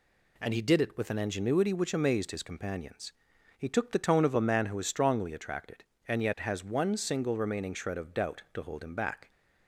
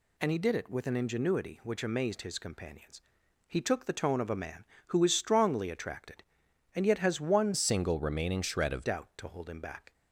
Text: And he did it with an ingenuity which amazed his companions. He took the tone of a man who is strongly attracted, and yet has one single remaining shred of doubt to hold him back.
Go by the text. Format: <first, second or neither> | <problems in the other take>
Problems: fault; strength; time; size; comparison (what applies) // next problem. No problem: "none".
first | changes voice from "single" to "of"; from 7.5 to 8.8 s; 1.3 s long